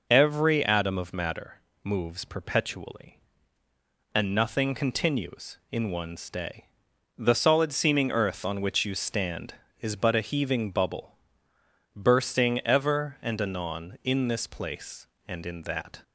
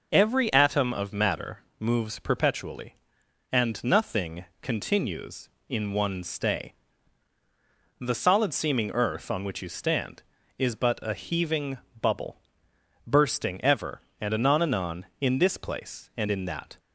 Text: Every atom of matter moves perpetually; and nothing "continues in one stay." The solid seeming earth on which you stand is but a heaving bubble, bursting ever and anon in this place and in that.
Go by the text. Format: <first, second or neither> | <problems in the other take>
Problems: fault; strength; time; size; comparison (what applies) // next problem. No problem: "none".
first | pauses between "matter" and "moves"; slight; at 1.5 s; 0.20 s long; slight in the first // pauses between "nothing" and "continues"; slight; at 4.4 s; 0.16 s long // pauses between "heaving" and "bubble"; slight; at 11.7 s; 0.24 s long // says "anon" twice; at 14.6 s